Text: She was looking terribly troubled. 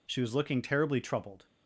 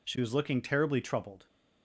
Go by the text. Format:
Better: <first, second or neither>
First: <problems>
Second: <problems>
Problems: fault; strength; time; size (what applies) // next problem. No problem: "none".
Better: neither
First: none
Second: none